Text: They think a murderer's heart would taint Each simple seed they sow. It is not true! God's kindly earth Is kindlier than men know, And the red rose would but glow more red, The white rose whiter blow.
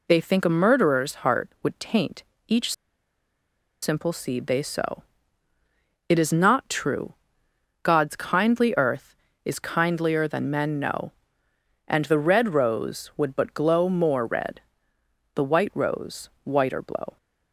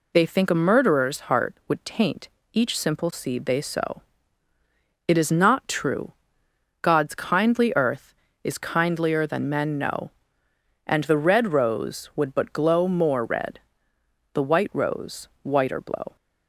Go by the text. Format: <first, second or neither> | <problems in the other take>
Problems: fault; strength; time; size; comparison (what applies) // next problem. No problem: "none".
second | pauses between "taint" and "Each"; slight; at 2.2 s; 0.26 s long; slight in the second // pauses between "Each" and "simple"; at 2.7 s; 1.0 s long // pauses between "rose" and "whiter"; slight; at 16.2 s; 0.16 s long; slight in the second